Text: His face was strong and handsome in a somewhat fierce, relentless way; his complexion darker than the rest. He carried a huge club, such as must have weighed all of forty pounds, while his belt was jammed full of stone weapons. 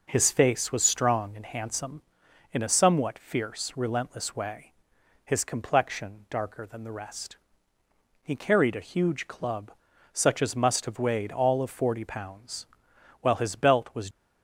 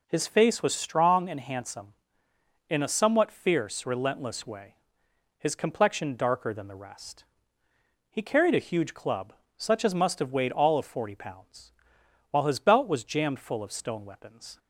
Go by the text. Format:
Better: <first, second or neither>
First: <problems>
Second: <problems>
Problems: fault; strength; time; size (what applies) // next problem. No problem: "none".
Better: second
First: stops before "jammed full of stone weapons"; at 14.1 s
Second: none